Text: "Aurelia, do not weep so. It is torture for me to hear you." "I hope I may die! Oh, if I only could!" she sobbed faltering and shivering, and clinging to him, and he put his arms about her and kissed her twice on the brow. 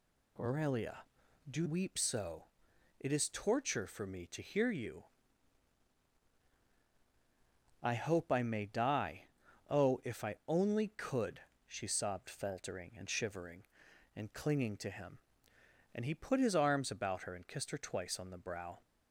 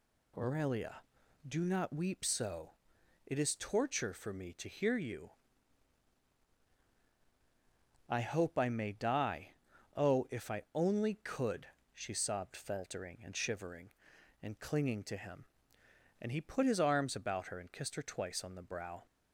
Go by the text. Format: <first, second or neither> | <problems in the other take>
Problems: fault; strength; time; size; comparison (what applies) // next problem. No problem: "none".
second | skips "not"; at 1.6 s